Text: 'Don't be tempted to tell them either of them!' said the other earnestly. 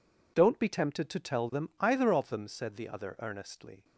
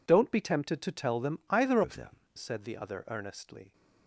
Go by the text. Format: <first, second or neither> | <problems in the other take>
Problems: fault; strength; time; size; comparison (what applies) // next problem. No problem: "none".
first | changes voice from "of" to "them"; from 1.8 to 2.1 s; 0.3 s long